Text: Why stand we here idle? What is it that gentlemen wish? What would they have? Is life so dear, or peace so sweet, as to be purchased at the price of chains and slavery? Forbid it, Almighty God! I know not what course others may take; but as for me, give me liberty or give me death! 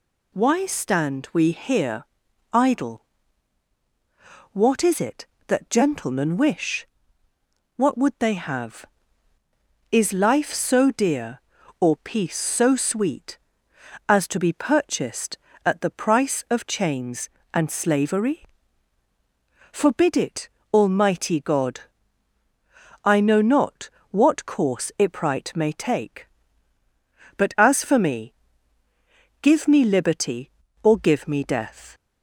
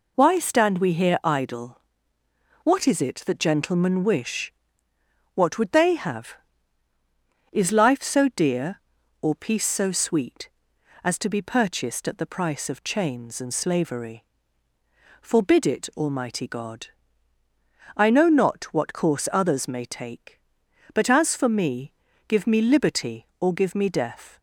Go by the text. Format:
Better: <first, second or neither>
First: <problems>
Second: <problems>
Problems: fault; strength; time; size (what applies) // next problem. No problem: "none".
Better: second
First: pauses between "here" and "idle"; noticeable; at 2.0 s; 0.48 s long // pauses between "not" and "what"; slight; at 23.8 s; 0.22 s long // says "ipright" for "others"; at 24.9 s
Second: none